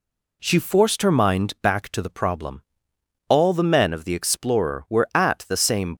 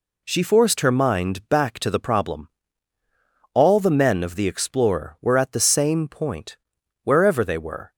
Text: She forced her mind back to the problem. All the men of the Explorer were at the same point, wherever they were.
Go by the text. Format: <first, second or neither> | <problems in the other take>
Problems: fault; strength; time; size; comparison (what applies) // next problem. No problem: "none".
second | stops before "point wherever they were"; at 5.9 s